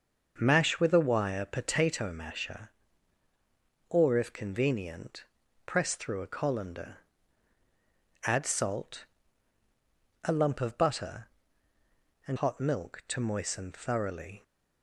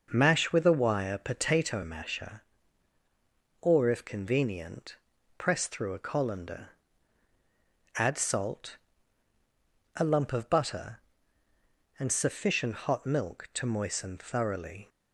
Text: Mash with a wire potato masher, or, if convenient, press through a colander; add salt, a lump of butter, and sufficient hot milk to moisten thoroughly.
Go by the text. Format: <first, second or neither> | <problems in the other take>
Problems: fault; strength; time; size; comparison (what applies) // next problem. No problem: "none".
second | starts louder than the rest; until 1.3 s; 6.5 dB // skips "sufficient"; at 12.3 s